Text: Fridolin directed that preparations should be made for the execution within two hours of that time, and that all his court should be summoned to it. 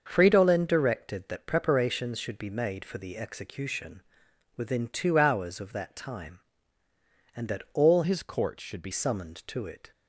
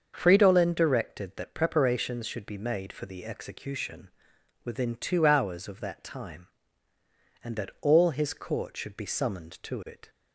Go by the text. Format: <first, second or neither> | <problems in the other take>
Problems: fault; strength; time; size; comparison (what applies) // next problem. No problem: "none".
second | starts louder than the rest; until 1.0 s; 6.5 dB; also in the second // pauses between "execution" and "within"; noticeable; at 4.0 s; 0.54 s long; noticeable in the second // changes voice from "his" to "be"; from 8.0 to 8.9 s; 0.9 s long